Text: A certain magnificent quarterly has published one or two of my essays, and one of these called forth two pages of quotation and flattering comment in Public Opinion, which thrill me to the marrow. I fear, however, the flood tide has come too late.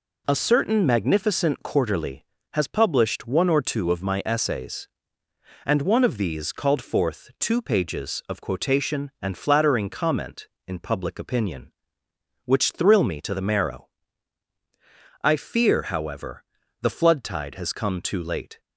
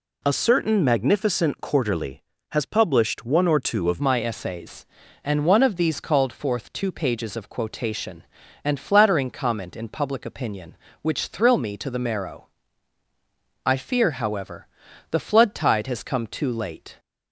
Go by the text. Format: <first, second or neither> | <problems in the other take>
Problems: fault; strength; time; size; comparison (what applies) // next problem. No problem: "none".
first | changes voice at "my"; from 3.9 s on; 13.0 s long